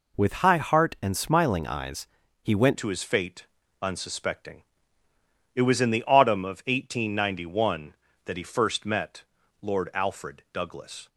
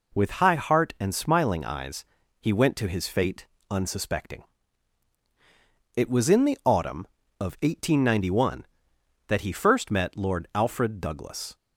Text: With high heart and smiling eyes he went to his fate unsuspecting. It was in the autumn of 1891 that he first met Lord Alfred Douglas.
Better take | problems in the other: second | pauses between "eyes" and "he"; slight; at 2.0 s; 0.34 s long; slight in the second // changes voice at "to"; from 2.7 s on; 8.3 s long // pauses between "fate" and "unsuspecting"; slight; at 3.4 s; 0.34 s long; slight in the second // pauses between "met" and "Lord"; slight; at 9.2 s; 0.36 s long

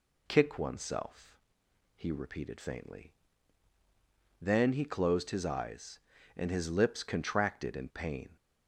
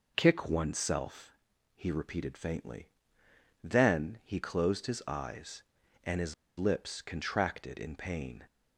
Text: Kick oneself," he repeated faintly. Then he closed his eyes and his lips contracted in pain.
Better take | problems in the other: first | pauses between "his" and "lips"; slight; at 6.3 s; 0.23 s long

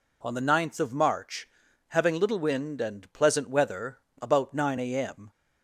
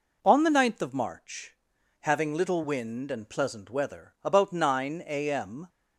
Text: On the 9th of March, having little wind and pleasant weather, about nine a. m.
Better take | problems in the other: neither | none

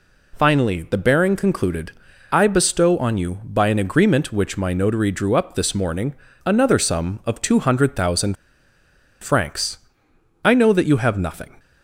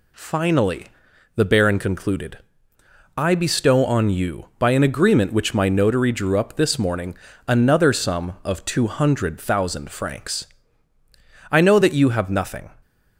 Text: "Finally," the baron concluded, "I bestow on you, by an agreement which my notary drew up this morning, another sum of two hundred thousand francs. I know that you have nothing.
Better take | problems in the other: second | pauses between "thousand" and "francs"; noticeable; at 8.3 s; 0.86 s long

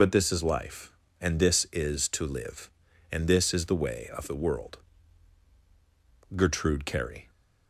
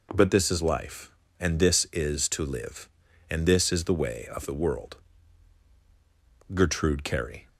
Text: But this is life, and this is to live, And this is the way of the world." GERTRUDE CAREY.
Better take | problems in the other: second | loses the start of "But"; at 0.0 s; 105 ms

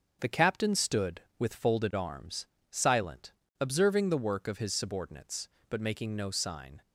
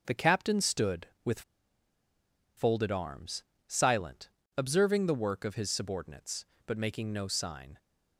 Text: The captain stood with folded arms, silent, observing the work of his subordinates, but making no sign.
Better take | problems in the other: first | starts louder than the rest; until 1.0 s; 7 dB; also in the first // pauses between "with" and "folded"; at 1.4 s; 1.1 s long

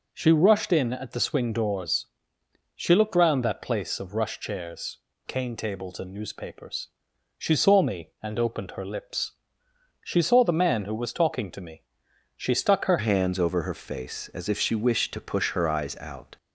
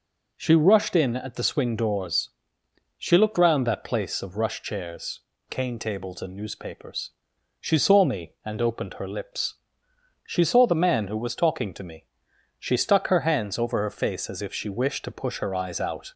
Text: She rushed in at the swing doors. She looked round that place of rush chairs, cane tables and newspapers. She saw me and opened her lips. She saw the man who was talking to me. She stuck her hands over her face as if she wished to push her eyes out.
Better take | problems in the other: second | changes voice at "hands"; from 12.9 s on; 3.4 s long

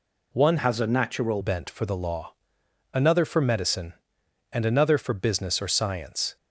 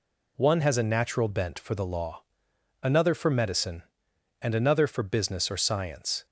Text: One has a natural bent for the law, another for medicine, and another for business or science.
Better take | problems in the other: second | changes voice from "has" to "natural"; from 0.5 to 1.4 s; 0.9 s long

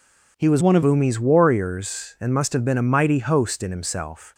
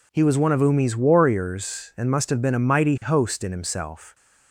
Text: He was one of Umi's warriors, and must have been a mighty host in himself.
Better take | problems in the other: second | changes voice from "one" to "of"; from 0.5 to 0.8 s; 0.3 s long

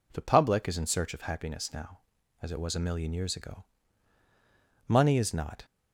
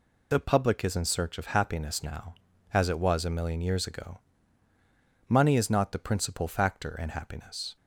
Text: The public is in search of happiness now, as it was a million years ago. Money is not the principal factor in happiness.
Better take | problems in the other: second | stops before "the principal factor in happiness"; at 5.6 s

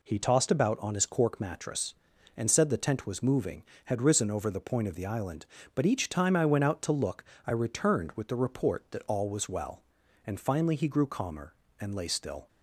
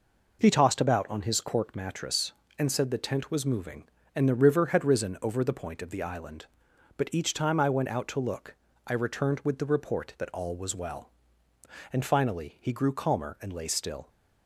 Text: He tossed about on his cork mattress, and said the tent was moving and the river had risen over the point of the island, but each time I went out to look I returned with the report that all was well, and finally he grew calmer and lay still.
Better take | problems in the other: second | skips "and the river"; at 3.7 s // pauses between "look" and "I"; slight; at 7.2 s; 0.22 s long; slight in the second

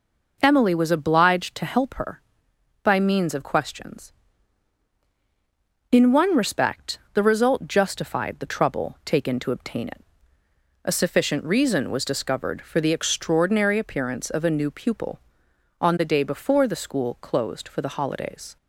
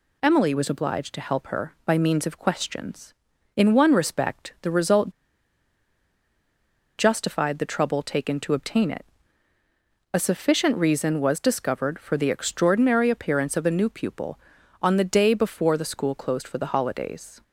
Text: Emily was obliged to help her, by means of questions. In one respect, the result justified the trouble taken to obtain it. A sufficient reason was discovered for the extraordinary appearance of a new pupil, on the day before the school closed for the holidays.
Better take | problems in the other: first | pauses between "result" and "justified"; strong; at 5.1 s; 1.8 s long

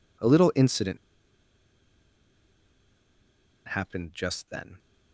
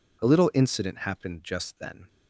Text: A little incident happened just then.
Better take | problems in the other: second | pauses between "incident" and "happened"; strong; at 0.9 s; 2.7 s long

